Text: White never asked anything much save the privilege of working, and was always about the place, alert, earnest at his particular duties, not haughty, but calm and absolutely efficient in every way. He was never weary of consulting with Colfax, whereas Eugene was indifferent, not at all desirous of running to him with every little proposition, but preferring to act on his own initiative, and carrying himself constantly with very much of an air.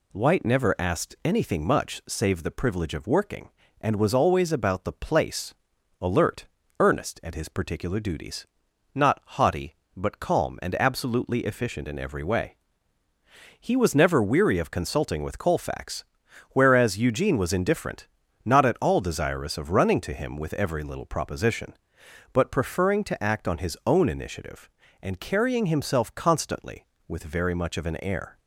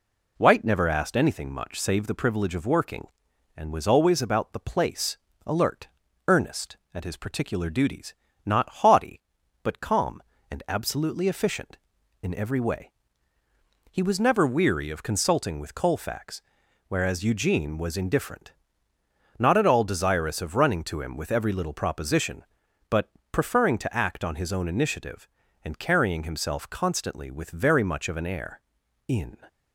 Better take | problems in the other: first | pauses between "but" and "preferring"; slight; at 23.0 s; 0.22 s long // goes on to say "In"; slight; from 29.0 s on; 0.30 s long

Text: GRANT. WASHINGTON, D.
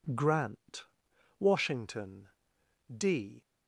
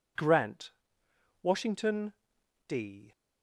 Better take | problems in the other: neither | none

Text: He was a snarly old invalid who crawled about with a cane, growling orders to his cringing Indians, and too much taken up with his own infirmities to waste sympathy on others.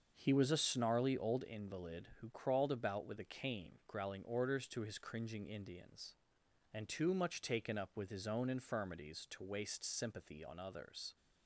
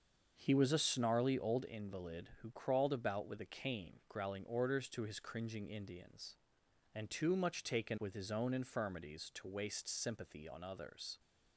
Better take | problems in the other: first | starts louder than the rest; until 1.3 s; 6.5 dB; also in the first // skips "up"; at 7.9 s

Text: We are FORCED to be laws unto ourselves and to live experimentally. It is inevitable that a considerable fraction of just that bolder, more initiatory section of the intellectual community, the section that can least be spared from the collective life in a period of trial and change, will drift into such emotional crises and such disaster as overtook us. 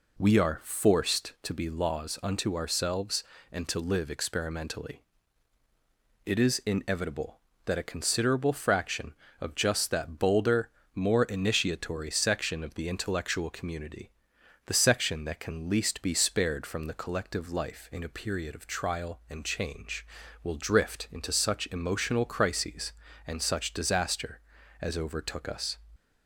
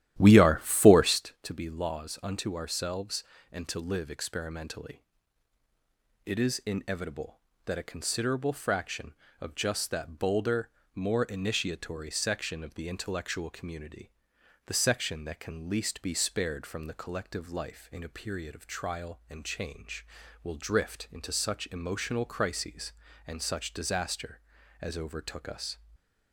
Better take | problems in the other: first | starts louder than the rest; strong; until 1.2 s; 12.5 dB // stays silent after the last word; slight; from 25.7 s on; 0.6 s long

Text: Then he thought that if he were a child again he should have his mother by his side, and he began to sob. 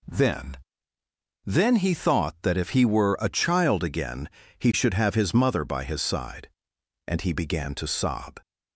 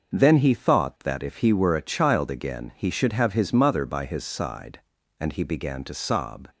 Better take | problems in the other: second | says "Then" twice; at 1.4 s // pauses between "again" and "he"; slight; at 4.2 s; 0.28 s long

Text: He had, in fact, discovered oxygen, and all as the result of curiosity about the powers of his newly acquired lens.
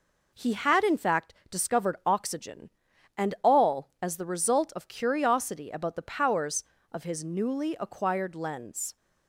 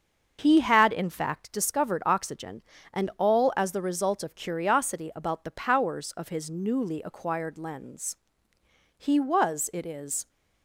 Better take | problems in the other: first | starts louder than the rest; until 1.4 s; 6.5 dB // goes on to say "He was it is"; noticeable; from 9.0 s on; 1.2 s long

